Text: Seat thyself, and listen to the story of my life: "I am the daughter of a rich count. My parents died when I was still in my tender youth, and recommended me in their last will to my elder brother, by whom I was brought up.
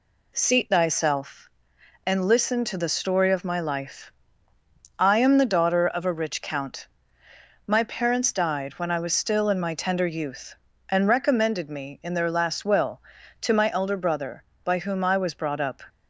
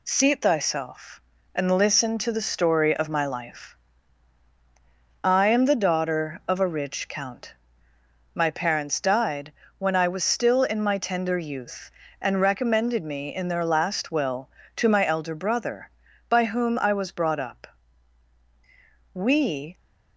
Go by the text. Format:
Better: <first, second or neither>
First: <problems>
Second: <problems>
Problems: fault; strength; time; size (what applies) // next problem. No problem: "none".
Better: first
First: none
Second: pauses between "died" and "when"; slight; at 9.5 s; 0.26 s long // goes on to say "We"; noticeable; from 19.1 s on; 0.64 s long